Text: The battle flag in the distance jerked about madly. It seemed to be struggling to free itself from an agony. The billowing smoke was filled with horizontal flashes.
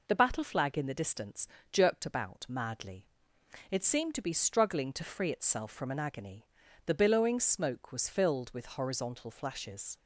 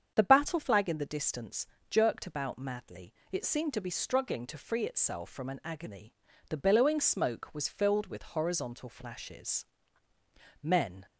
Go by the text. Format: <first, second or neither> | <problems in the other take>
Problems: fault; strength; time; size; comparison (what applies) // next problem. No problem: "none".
first | starts louder than the rest; strong; until 1.1 s; 7.5 dB // pauses between "distance" and "jerked"; slight; at 1.6 s; 0.24 s long; slight in the first // goes on to say "Men"; slight; from 10.6 s on; 0.44 s long